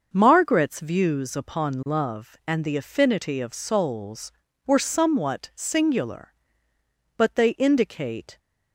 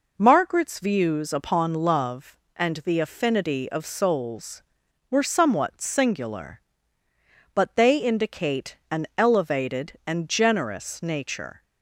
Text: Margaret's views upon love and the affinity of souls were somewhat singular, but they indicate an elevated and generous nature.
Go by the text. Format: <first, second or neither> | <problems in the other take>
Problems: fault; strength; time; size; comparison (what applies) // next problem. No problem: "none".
second | starts louder than the rest; until 1.1 s; 6 dB // stops before "an elevated and generous nature"; at 8.3 s